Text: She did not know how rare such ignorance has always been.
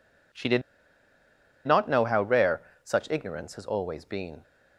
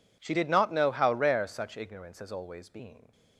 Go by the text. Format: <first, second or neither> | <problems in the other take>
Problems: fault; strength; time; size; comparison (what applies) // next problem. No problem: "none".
second | pauses between "did" and "not"; at 0.6 s; 1.0 s long // pauses between "rare" and "such"; slight; at 2.6 s; 0.20 s long